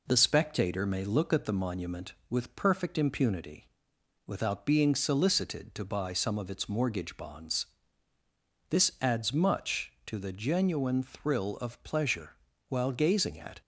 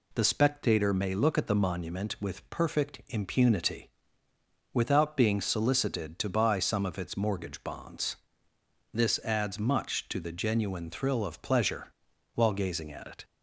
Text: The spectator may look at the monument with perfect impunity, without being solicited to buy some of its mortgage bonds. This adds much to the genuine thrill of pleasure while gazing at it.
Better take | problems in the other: second | pauses between "pleasure" and "while"; slight; at 12.3 s; 0.32 s long; also in the second // stops before "it"; at 13.6 s

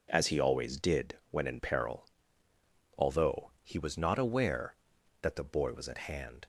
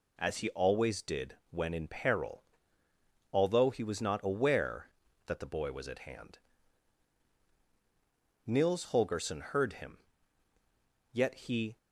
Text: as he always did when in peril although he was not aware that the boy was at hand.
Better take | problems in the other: first | pauses between "peril" and "although"; noticeable; at 2.4 s; 0.90 s long; noticeable in the first // goes on to say "Nils Holgersson heard him yet he"; strong; from 8.4 s on; 3.3 s long

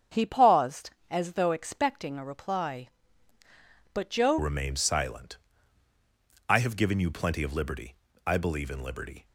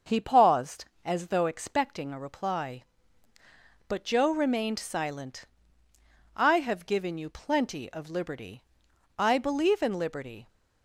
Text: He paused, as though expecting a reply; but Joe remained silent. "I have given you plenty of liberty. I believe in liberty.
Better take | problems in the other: second | starts louder than the rest; strong; until 1.3 s; 7.5 dB; also in the second // changes voice at "remained"; from 4.3 s on; 4.9 s long

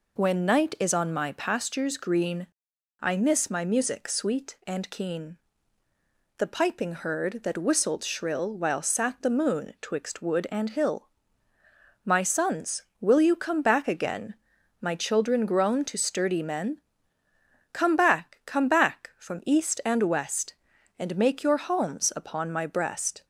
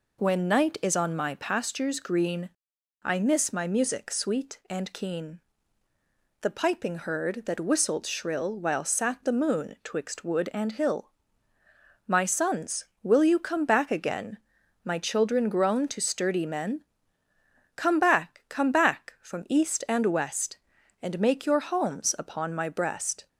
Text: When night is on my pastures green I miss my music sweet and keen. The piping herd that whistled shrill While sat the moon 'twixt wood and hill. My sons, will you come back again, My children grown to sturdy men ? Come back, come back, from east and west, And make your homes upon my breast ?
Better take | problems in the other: neither | pauses between "green" and "I"; noticeable; the same in both

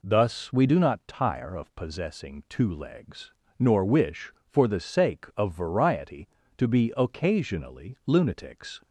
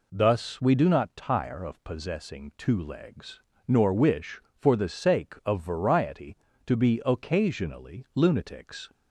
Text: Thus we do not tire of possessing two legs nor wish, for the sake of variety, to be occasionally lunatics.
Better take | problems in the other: neither | pauses between "legs" and "nor"; slight; the same in both

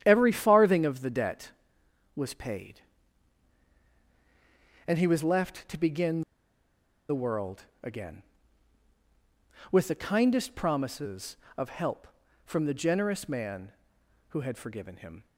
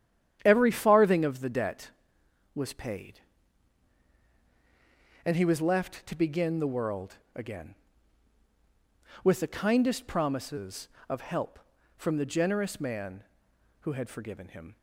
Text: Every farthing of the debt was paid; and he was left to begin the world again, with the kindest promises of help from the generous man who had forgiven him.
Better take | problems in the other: second | starts louder than the rest; strong; until 1.0 s; 10 dB; strong in the second // pauses between "begin" and "the"; noticeable; at 6.2 s; 0.87 s long // pauses between "world" and "again"; slight; at 7.6 s; 0.20 s long; slight in the second

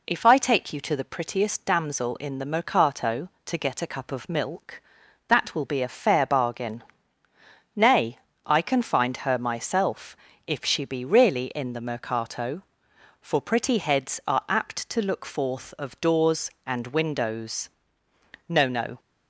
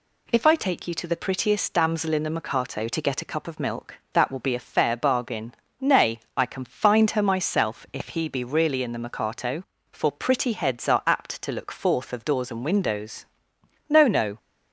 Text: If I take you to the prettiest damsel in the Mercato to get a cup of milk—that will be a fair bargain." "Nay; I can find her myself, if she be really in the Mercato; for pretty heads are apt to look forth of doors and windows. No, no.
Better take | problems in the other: first | says "he" for "she"; at 8.0 s

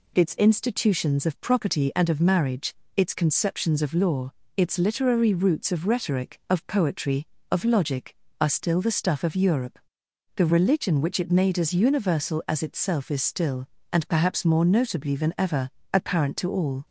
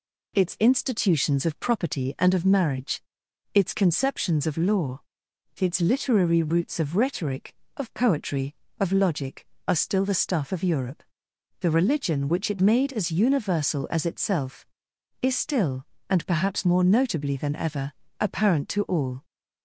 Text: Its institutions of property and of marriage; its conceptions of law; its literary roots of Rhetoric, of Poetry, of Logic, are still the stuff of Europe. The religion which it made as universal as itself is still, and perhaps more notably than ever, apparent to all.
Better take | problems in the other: neither | none

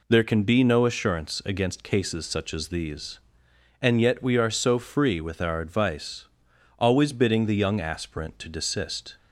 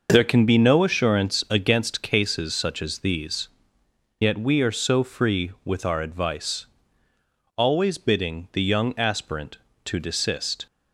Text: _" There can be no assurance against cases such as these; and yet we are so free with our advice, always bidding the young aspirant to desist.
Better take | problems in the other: first | skips "and"; at 3.8 s

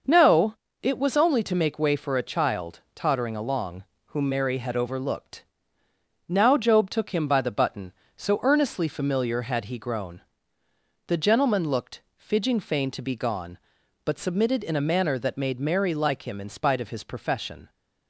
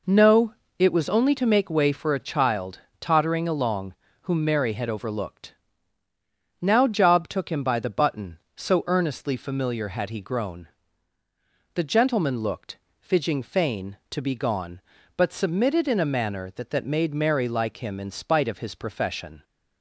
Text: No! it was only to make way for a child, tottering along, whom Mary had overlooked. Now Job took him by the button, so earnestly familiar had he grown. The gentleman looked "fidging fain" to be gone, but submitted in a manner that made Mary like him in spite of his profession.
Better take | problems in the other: first | pauses between "looked" and "fidging"; slight; at 12.7 s; 0.22 s long; slight in the first // says "that" twice; at 16.7 s

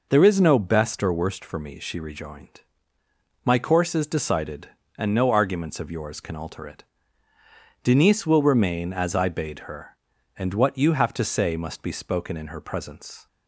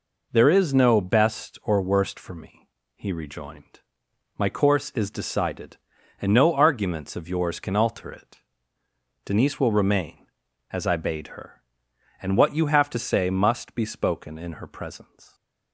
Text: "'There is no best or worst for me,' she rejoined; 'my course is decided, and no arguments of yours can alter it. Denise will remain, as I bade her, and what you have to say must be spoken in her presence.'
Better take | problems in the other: first | says "he" for "she"; at 2.9 s

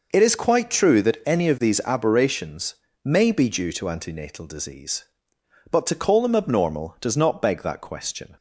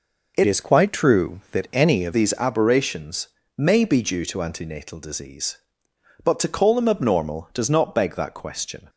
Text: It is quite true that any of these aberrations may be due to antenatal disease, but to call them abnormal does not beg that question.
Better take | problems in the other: first | changes voice from "is" to "of"; from 0.4 to 2.1 s; 1.7 s long // pauses between "aberrations" and "may"; slight; at 3.2 s; 0.30 s long; slight in the first

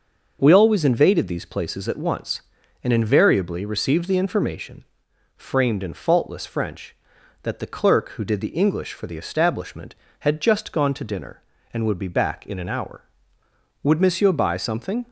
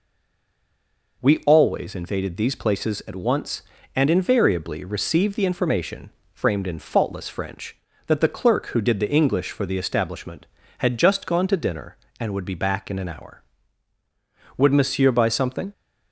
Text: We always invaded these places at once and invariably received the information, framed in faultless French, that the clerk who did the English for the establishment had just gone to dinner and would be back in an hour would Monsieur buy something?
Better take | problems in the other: first | stays silent before the first word; noticeable; until 1.2 s; 1.2 s long

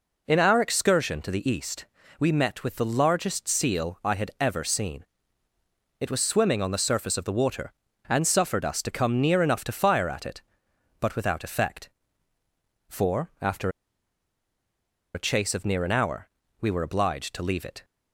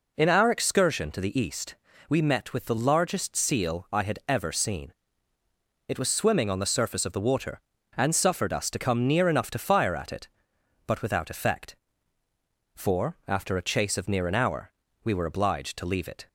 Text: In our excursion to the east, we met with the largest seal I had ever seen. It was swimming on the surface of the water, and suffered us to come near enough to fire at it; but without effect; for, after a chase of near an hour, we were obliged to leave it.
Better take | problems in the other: second | pauses between "after" and "a"; strong; at 13.6 s; 1.4 s long

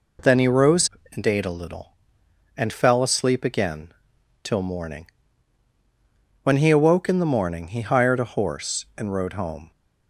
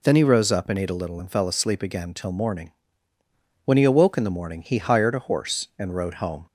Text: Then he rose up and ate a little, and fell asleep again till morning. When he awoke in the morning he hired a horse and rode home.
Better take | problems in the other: second | skips "up"; at 1.0 s // pauses between "again" and "till"; noticeable; at 3.9 s; 0.52 s long

